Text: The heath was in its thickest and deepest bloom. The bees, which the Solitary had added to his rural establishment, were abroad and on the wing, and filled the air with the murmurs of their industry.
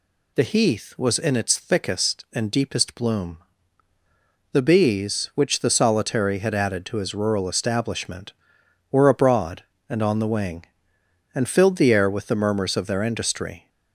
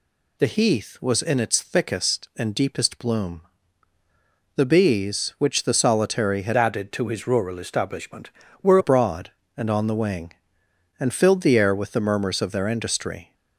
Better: first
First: none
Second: changes voice from "added" to "were"; from 6.5 to 8.7 s; 2.2 s long

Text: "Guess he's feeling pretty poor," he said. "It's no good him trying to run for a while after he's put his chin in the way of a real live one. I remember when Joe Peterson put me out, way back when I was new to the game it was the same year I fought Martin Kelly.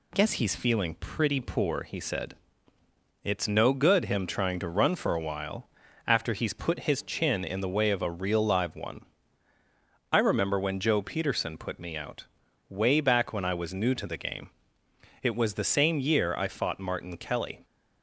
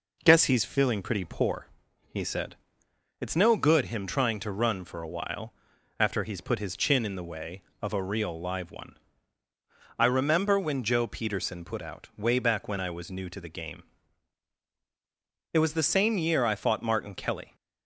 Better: first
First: pauses between "while" and "after"; slight; at 5.6 s; 0.36 s long // pauses between "game" and "it"; noticeable; at 14.5 s; 0.72 s long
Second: pauses between "while" and "after"; at 5.5 s; 0.44 s long // skips "me"; at 11.8 s // pauses between "game" and "it"; strong; at 13.8 s; 1.7 s long

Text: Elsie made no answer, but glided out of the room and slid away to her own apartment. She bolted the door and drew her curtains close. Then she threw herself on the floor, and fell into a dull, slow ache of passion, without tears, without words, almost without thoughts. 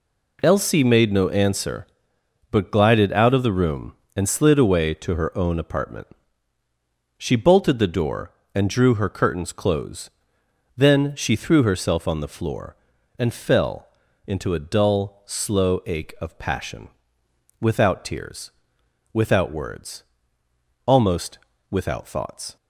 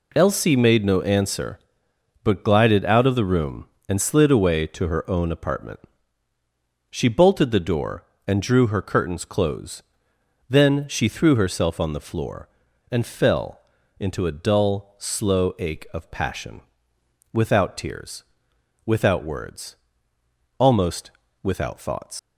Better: first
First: pauses between "fell" and "into"; at 13.8 s; 0.38 s long // pauses between "almost" and "without"; slight; at 21.3 s; 0.32 s long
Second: pauses between "fell" and "into"; at 13.6 s; 0.38 s long // pauses between "almost" and "without"; slight; at 21.1 s; 0.32 s long // leaves "thoughts" unfinished; at 22.1 s; 90 ms

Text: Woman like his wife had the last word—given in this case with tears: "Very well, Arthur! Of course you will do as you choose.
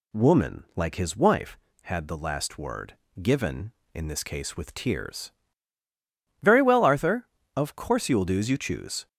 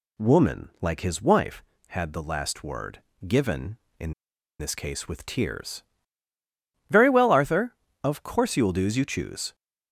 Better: first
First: none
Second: pauses between "in" and "this"; noticeable; at 4.1 s; 0.46 s long

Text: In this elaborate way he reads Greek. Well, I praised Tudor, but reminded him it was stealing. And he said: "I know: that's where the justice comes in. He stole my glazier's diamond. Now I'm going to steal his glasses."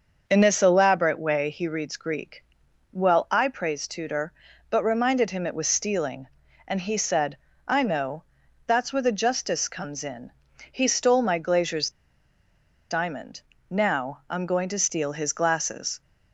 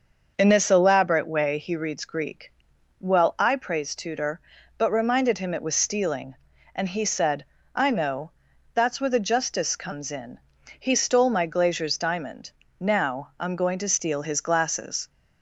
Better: second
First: starts louder than the rest; until 1.2 s; 6 dB // pauses between "glazier's" and "diamond"; at 11.9 s; 0.98 s long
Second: starts louder than the rest; until 1.3 s; 6 dB

